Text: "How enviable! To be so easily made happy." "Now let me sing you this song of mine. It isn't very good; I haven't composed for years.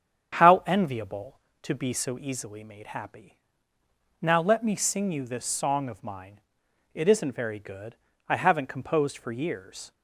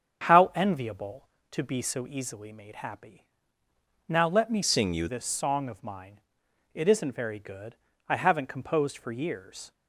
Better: first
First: starts louder than the rest; strong; until 1.6 s; 8 dB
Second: starts louder than the rest; strong; until 1.5 s; 7.5 dB // changes voice from "sing" to "you"; from 4.6 to 5.0 s; 0.4 s long

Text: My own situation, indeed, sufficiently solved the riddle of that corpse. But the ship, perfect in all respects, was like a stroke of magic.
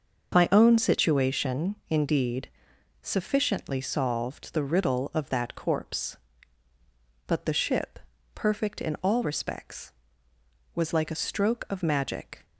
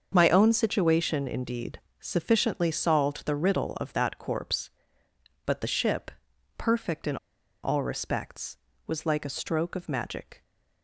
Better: first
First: starts louder than the rest; until 1.3 s; 6 dB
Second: starts louder than the rest; until 1.1 s; 6.5 dB // pauses between "in" and "all"; noticeable; at 7.1 s; 0.46 s long

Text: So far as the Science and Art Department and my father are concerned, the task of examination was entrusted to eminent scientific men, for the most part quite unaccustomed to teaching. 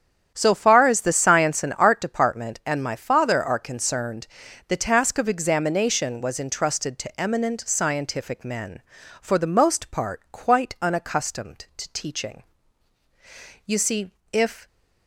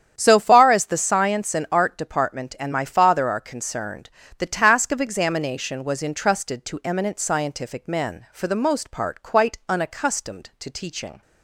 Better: second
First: starts louder than the rest; strong; until 1.3 s; 9 dB // goes on to say "You see if"; noticeable; from 13.6 s on; 1.0 s long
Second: starts louder than the rest; strong; until 1.1 s; 9 dB

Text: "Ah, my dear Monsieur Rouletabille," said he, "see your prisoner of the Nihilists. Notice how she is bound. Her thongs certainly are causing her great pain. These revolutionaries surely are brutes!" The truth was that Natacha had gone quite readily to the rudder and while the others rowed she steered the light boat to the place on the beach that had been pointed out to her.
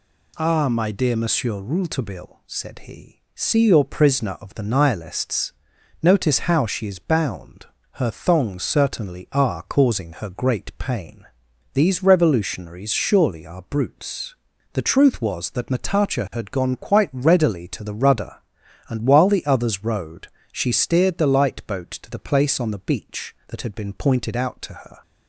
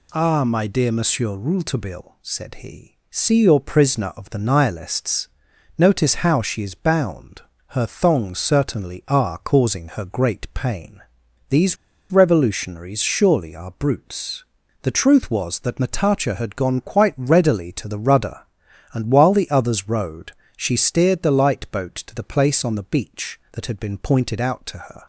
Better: first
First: pauses between "rowed" and "she"; slight; at 20.2 s; 0.26 s long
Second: pauses between "These" and "revolutionaries"; slight; at 11.7 s; 0.35 s long // pauses between "rowed" and "she"; slight; at 20.3 s; 0.26 s long

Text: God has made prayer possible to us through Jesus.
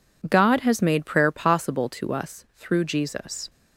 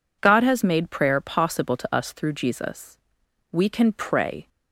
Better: first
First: none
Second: goes on to say "We can pray"; noticeable; from 3.5 s on; 0.96 s long

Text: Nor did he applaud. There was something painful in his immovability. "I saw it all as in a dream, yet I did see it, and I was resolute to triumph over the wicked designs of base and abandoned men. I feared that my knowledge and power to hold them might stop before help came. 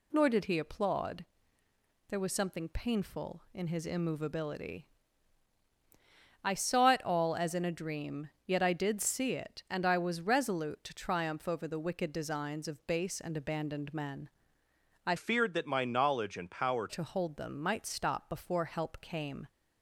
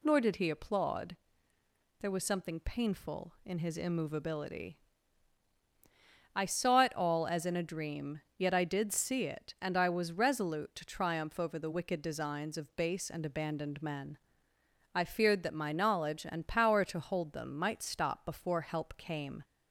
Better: second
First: changes voice from "feared" to "power"; from 15.1 to 16.8 s; 1.7 s long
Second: none

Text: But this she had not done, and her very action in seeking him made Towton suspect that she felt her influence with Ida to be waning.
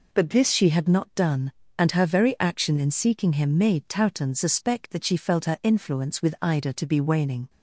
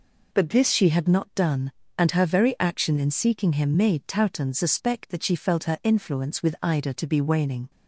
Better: neither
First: none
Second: none

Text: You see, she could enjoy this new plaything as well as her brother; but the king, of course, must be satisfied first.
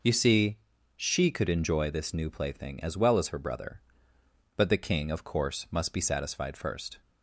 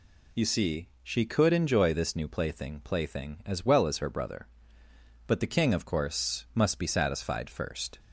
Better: first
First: none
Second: says "plaything" twice; at 2.8 s

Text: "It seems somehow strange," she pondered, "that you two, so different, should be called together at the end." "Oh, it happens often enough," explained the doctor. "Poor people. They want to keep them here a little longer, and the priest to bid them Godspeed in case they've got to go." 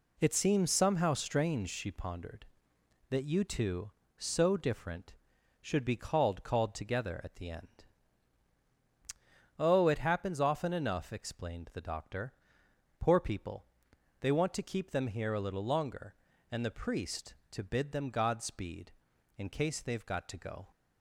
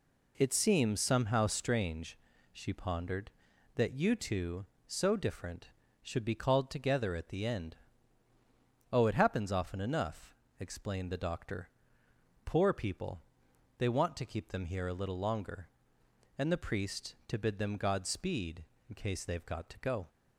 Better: second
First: says "called" twice; at 6.4 s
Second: none

